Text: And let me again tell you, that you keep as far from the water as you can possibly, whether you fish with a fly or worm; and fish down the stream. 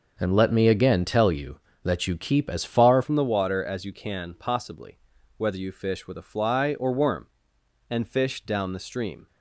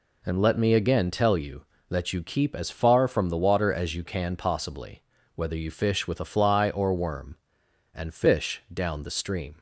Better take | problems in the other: second | starts louder than the rest; noticeable; until 1.1 s; 6 dB // changes voice at "from"; from 3.0 s on; 6.2 s long

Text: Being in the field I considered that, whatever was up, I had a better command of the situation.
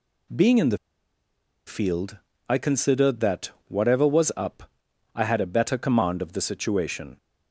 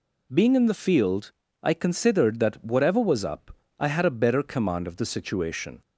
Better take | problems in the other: second | pauses between "the" and "field"; noticeable; at 0.7 s; 0.89 s long // pauses between "field" and "I"; slight; at 2.1 s; 0.32 s long; slight in the second

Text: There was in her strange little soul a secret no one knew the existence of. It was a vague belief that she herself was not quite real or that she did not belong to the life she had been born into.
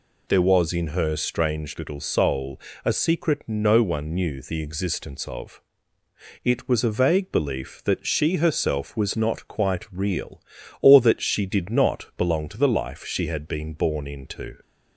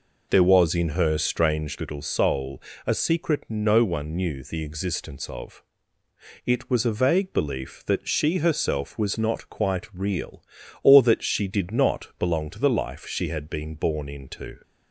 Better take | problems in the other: first | starts louder than the rest; noticeable; until 2.2 s; 4.5 dB // pauses between "soul" and "a"; slight; at 2.6 s; 0.24 s long; slight in the first

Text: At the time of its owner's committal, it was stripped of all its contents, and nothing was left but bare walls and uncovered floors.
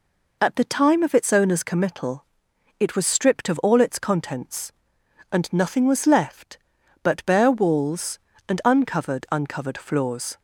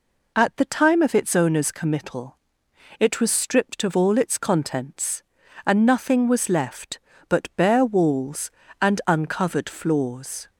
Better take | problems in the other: second | says "uncovered" twice; at 9.3 s

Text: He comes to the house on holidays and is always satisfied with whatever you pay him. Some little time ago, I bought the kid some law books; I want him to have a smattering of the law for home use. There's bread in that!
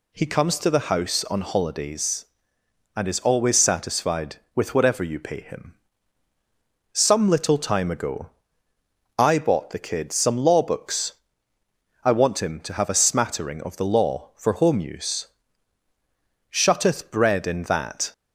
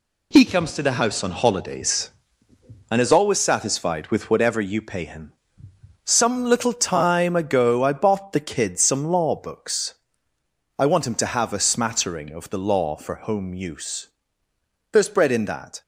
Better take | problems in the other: second | says "Shutteth" for "There's"; at 16.5 s

